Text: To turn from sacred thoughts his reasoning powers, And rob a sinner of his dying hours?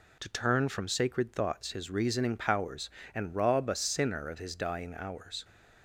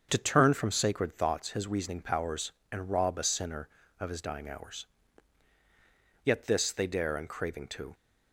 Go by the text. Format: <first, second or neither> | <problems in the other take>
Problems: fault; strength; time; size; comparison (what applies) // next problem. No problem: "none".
first | starts louder than the rest; strong; until 1.1 s; 7 dB // goes on to say "Yet this they dare and craving to"; strong; from 6.2 s on; 1.7 s long